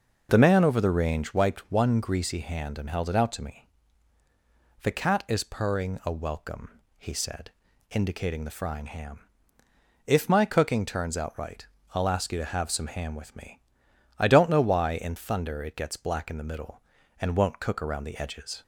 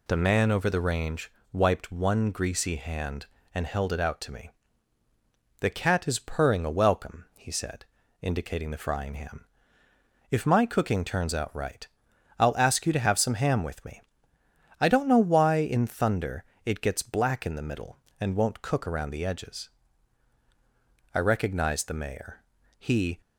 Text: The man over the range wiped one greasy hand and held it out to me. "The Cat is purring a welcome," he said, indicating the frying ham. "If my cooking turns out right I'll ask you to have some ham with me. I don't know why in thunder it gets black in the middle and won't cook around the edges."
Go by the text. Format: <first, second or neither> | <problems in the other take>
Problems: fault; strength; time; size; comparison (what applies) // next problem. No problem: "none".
first | pauses between "range" and "wiped"; slight; at 1.2 s; 0.22 s long // pauses between "right" and "I'll"; noticeable; at 11.8 s; 0.54 s long; slight in the first // pauses between "thunder" and "it"; slight; at 16.4 s; 0.22 s long // goes on to say "I recognized the mayor He"; strong; from 21.1 s on; 2.0 s long